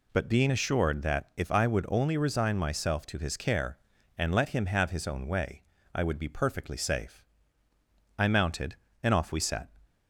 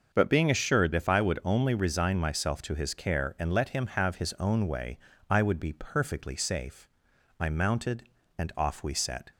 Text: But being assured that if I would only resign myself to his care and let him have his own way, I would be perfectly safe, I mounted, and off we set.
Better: first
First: none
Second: starts louder than the rest; until 1.1 s; 6.5 dB // skips "that"; at 0.9 s

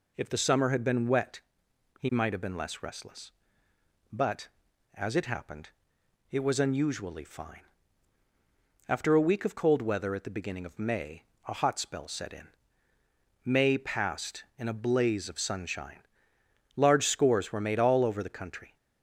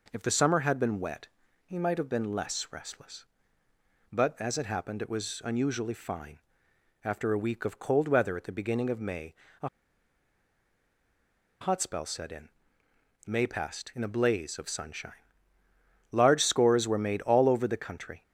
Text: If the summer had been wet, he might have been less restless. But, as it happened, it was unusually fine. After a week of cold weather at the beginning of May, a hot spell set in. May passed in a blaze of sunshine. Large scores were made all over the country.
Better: first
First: none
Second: pauses between "a" and "hot"; strong; at 9.6 s; 1.9 s long

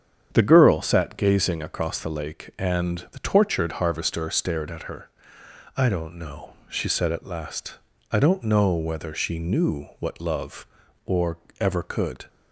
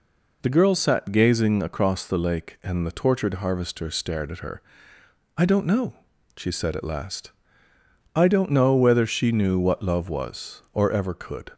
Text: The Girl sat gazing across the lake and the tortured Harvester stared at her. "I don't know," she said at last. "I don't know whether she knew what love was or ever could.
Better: second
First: starts louder than the rest; strong; until 1.3 s; 8 dB // skips "was"; at 10.8 s // pauses between "or" and "ever"; slight; at 11.3 s; 0.24 s long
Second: none

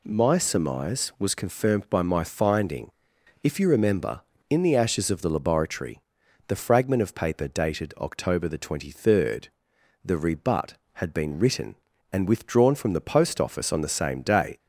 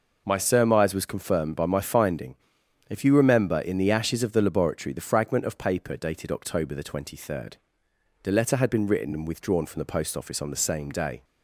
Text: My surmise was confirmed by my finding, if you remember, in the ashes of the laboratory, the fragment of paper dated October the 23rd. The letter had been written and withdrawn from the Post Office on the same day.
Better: second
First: says "rebut" for "letter"; at 10.1 s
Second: none

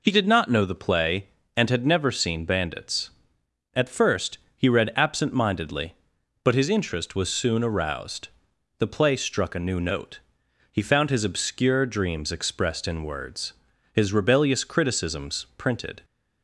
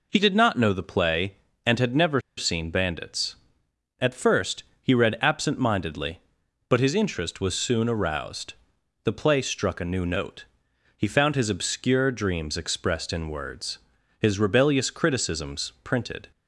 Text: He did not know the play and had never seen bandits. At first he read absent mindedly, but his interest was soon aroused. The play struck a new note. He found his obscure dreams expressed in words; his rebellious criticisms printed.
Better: first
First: pauses between "first" and "he"; slight; at 4.3 s; 0.18 s long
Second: pauses between "never" and "seen"; slight; at 2.1 s; 0.18 s long // pauses between "first" and "he"; slight; at 4.6 s; 0.18 s long

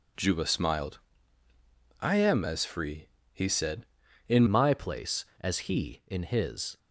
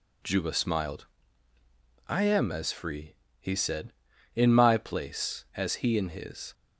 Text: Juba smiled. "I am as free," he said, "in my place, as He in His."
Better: second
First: changes voice at "my"; from 4.4 s on; 2.3 s long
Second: none

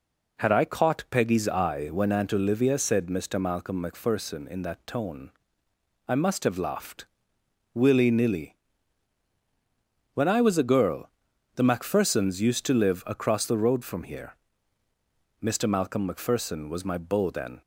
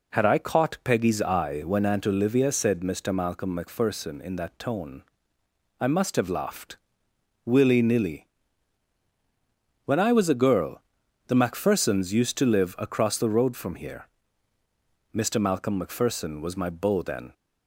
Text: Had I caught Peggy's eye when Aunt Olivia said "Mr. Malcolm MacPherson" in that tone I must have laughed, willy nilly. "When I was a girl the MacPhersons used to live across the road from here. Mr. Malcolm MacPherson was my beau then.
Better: neither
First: pauses between "tone" and "I"; noticeable; at 5.2 s; 0.78 s long // pauses between "girl" and "the"; noticeable; at 11.0 s; 0.46 s long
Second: pauses between "tone" and "I"; noticeable; at 5.0 s; 0.78 s long // pauses between "girl" and "the"; noticeable; at 10.8 s; 0.46 s long

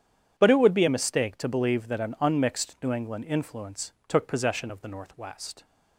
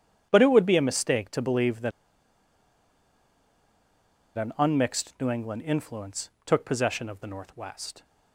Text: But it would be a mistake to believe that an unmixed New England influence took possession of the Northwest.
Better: first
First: starts louder than the rest; strong; until 1.3 s; 9 dB // pauses between "influence" and "took"; slight; at 3.9 s; 0.16 s long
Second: starts louder than the rest; strong; until 1.3 s; 9 dB // pauses between "that" and "an"; strong; at 1.9 s; 2.4 s long // pauses between "influence" and "took"; slight; at 6.2 s; 0.16 s long

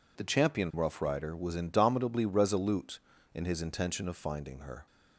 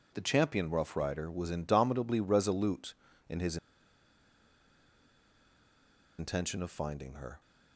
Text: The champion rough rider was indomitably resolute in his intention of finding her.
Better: first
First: none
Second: pauses between "his" and "intention"; strong; at 3.5 s; 2.6 s long

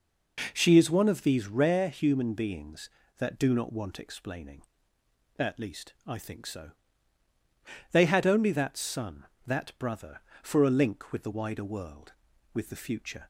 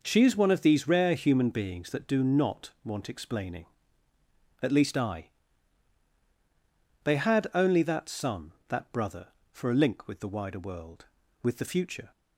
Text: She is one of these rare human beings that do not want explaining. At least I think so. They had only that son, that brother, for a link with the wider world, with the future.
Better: first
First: none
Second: skips "think so"; at 6.1 s

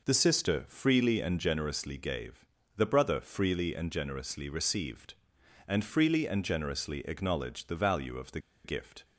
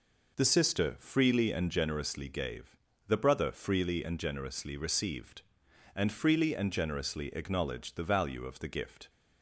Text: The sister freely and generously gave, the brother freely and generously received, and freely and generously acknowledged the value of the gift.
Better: second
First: pauses between "the" and "gift"; slight; at 8.3 s; 0.25 s long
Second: none

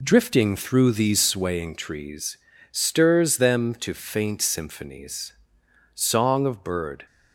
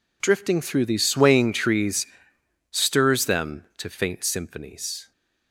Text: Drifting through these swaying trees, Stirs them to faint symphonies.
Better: second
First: goes on to say "Song of bird"; noticeable; from 5.9 s on; 1.1 s long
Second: none

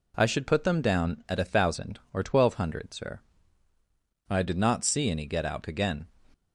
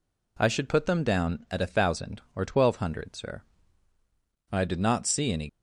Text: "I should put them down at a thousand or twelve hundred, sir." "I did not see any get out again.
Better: first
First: none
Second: stops before "get out again"; at 5.4 s

